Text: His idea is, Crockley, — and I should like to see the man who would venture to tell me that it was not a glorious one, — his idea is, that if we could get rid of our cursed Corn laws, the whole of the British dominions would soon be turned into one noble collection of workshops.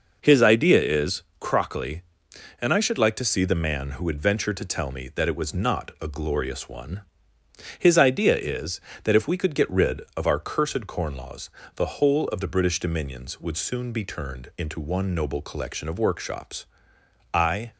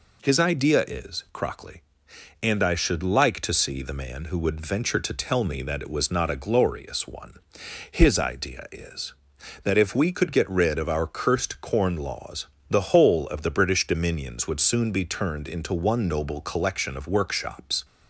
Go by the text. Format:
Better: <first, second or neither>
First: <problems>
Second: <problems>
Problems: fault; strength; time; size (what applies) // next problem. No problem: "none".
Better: second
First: goes on to say "I"; slight; from 17.3 s on; 0.38 s long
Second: none